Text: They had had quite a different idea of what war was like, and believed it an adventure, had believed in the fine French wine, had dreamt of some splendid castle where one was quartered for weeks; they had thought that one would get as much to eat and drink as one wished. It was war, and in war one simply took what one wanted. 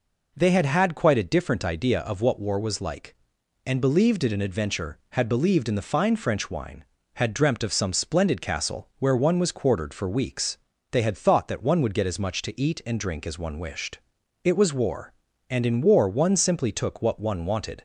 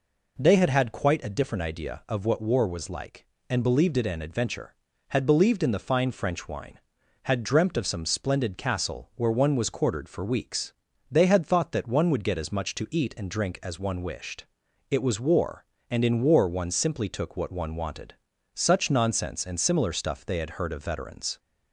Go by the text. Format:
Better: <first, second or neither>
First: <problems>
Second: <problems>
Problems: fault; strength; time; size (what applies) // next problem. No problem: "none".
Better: first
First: none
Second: goes on to say "Such nonsense and similar stuff they had heard of veterans"; strong; from 18.5 s on; 2.8 s long